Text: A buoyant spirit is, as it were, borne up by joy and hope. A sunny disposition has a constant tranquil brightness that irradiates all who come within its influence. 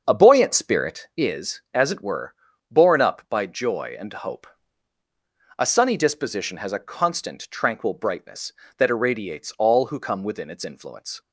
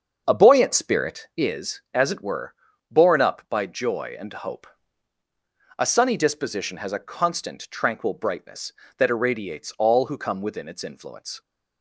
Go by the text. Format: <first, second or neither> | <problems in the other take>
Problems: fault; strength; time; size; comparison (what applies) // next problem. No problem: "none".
neither | starts louder than the rest; the same in both